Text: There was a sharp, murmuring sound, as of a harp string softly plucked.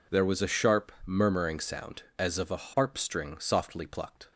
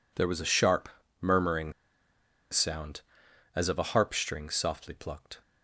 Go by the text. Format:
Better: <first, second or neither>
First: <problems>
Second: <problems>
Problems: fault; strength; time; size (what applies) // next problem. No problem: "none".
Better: first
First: none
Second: pauses between "murmuring" and "sound"; noticeable; at 1.7 s; 0.78 s long